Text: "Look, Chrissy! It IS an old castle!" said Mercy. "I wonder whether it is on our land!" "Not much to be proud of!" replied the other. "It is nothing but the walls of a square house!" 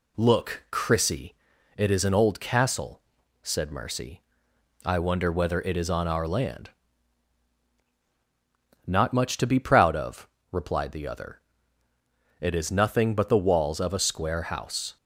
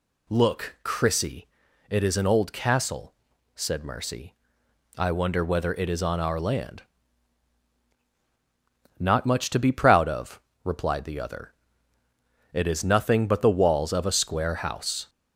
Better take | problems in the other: first | gets louder; slight; throughout; 2.5 dB

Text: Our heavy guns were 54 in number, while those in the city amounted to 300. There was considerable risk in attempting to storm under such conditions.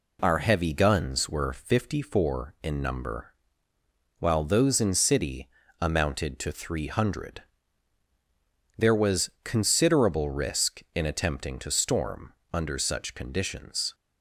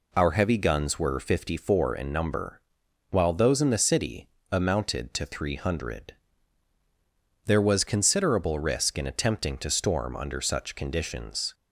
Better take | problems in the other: second | skips "the"; at 4.9 s // pauses between "city" and "amounted"; slight; at 5.4 s; 0.32 s long; slight in the second // pauses between "storm" and "under"; slight; at 12.3 s; 0.18 s long

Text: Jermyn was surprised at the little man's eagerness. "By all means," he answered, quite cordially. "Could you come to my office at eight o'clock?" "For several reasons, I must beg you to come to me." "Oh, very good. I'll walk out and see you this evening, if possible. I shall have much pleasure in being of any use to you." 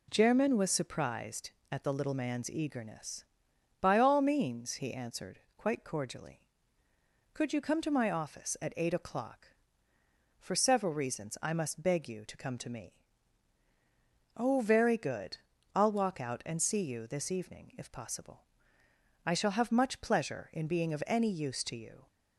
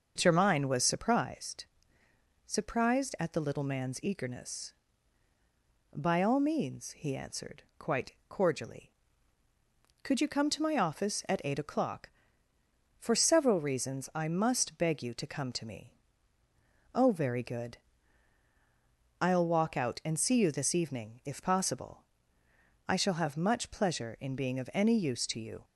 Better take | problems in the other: first | starts louder than the rest; until 1.1 s; 6 dB // says "surprised" twice; at 2.4 s // pauses between "quite" and "cordially"; slight; at 8.1 s; 0.16 s long

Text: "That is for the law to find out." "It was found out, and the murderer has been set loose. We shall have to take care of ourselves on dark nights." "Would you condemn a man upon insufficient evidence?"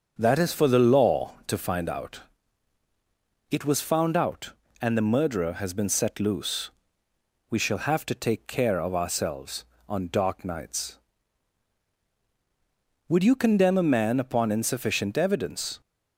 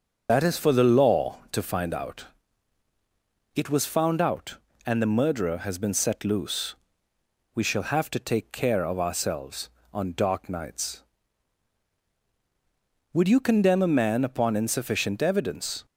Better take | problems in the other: first | loses the start of "That"; at 0.2 s; 65 ms // starts louder than the rest; until 1.3 s; 6.5 dB; also in the first

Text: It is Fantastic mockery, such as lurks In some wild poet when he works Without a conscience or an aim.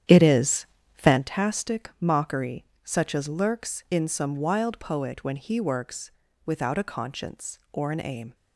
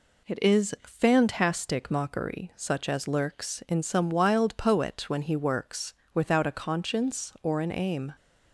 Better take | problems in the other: second | starts louder than the rest; strong; until 1.2 s; 9.5 dB // pauses between "is" and "Fantastic"; slight; at 0.6 s; 0.30 s long // pauses between "works" and "Without"; slight; at 6.1 s; 0.34 s long; slight in the second

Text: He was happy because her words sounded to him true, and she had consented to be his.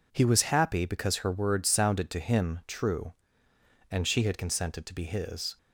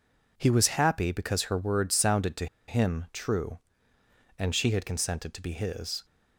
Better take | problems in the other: first | pauses between "to" and "him"; slight; at 2.4 s; 0.22 s long

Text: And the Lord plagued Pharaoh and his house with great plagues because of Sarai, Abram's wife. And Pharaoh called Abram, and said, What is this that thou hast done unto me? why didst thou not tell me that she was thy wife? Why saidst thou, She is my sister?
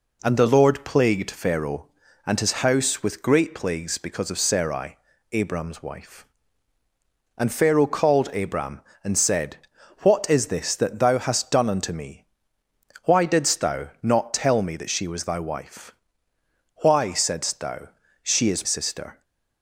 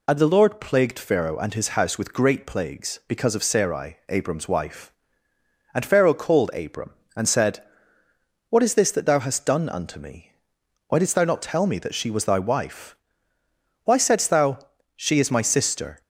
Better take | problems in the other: second | pauses between "thou" and "not"; slight; at 13.8 s; 0.16 s long // skips "my"; at 18.6 s

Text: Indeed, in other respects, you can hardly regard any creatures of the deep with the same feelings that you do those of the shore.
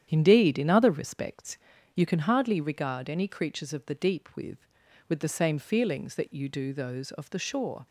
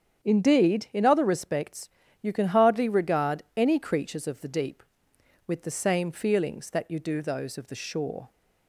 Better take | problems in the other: second | starts louder than the rest; strong; until 1.1 s; 9.5 dB; strong in the second // says "with" twice; at 5.0 s

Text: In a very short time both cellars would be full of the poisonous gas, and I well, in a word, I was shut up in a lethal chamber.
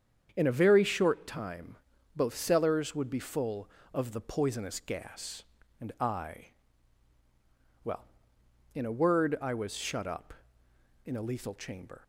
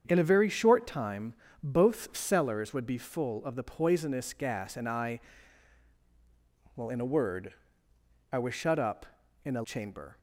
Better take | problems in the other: first | starts louder than the rest; strong; until 1.0 s; 7.5 dB; strong in the first // pauses between "time" and "both"; slight; at 1.3 s; 0.30 s long; also in the first // pauses between "I" and "well"; strong; at 5.1 s; 1.5 s long; strong in the first // skips "lethal"; at 9.6 s

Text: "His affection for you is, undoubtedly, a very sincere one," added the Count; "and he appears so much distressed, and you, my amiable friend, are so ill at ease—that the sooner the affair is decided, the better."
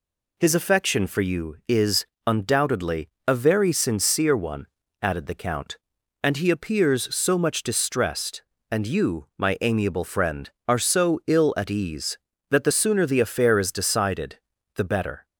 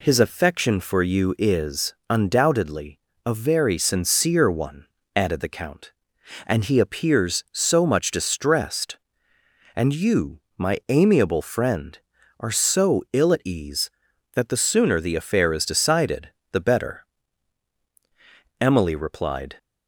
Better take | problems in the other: first | goes on to say "Emily replied"; noticeable; from 18.6 s on; 0.94 s long

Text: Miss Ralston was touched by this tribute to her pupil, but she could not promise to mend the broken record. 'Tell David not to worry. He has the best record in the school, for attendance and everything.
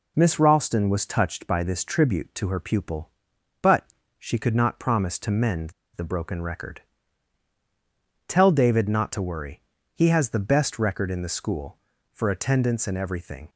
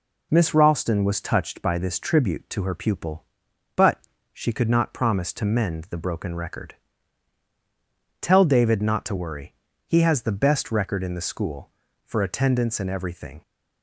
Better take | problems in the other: second | pauses between "but" and "she"; slight; at 3.8 s; 0.32 s long; slight in the second // pauses between "mend" and "the"; slight; at 5.7 s; 0.23 s long

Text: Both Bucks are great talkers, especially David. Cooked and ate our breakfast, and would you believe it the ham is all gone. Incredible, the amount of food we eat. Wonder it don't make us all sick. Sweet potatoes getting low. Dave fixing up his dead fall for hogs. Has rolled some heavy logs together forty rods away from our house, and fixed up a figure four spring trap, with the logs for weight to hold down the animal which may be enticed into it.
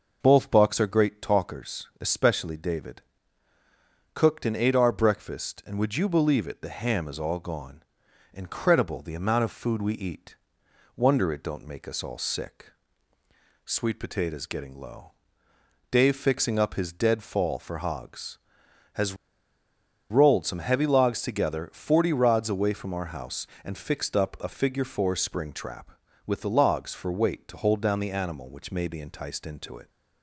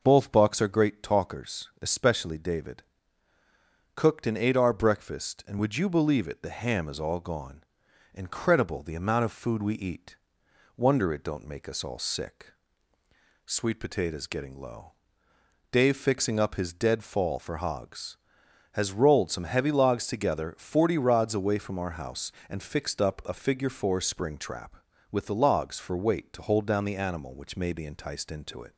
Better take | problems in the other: second | pauses between "Has" and "rolled"; noticeable; at 19.1 s; 0.95 s long

